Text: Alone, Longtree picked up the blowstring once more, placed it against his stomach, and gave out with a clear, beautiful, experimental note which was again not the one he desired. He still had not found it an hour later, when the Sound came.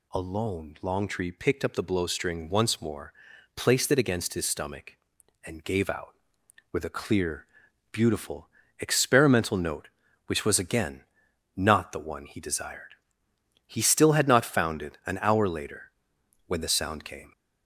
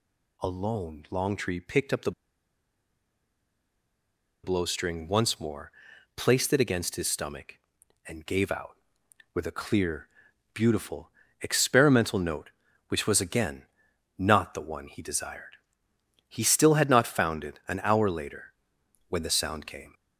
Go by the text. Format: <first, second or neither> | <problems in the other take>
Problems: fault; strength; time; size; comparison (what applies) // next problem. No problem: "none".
first | pauses between "the" and "blowstring"; strong; at 2.1 s; 2.3 s long // pauses between "again" and "not"; noticeable; at 13.6 s; 0.54 s long; noticeable in the first